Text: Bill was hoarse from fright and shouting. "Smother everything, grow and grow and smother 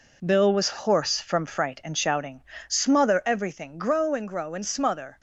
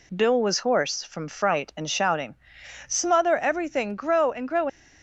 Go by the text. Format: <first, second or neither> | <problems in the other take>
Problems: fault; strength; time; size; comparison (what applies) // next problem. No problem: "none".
first | stops before "and smother"; at 4.6 s